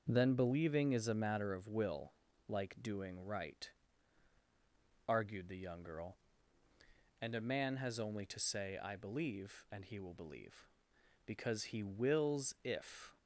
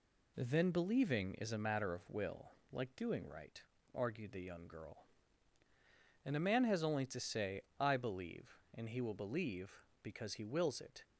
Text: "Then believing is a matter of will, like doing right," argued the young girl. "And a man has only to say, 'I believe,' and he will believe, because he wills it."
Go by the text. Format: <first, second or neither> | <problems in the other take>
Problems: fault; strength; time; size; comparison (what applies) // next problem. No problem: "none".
second | starts louder than the rest; until 1.0 s; 6.5 dB // says "if" for "it"; at 12.6 s